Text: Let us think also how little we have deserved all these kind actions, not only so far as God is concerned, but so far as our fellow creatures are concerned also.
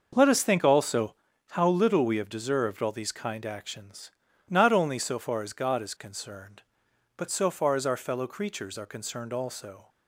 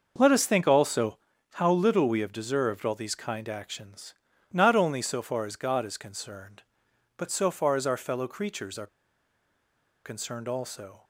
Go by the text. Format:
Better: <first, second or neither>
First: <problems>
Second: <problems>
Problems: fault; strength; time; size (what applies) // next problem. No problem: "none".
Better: first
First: starts louder than the rest; noticeable; until 1.1 s; 6 dB // pauses between "also" and "how"; slight; at 1.1 s; 0.34 s long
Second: starts louder than the rest; noticeable; until 1.1 s; 6 dB // pauses between "also" and "how"; slight; at 1.1 s; 0.34 s long // pauses between "are" and "concerned"; at 8.8 s; 1.1 s long